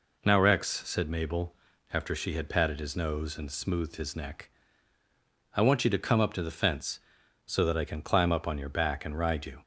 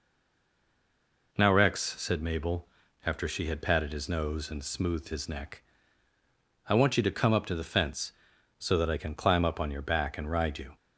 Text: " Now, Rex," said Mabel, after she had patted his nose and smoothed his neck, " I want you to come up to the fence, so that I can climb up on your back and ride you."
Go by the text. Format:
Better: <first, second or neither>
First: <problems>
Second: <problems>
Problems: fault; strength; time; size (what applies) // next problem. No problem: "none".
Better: first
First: none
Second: stays silent before the first word; noticeable; until 1.3 s; 1.3 s long